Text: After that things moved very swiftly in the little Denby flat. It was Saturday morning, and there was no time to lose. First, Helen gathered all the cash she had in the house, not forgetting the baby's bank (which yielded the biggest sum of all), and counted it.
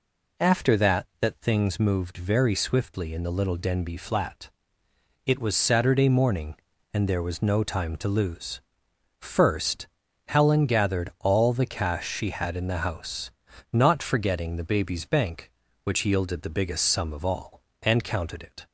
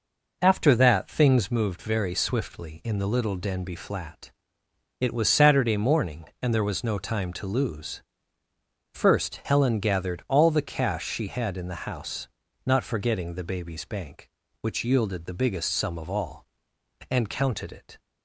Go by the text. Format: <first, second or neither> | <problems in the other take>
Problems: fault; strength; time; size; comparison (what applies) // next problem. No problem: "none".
second | says "that" twice; at 1.2 s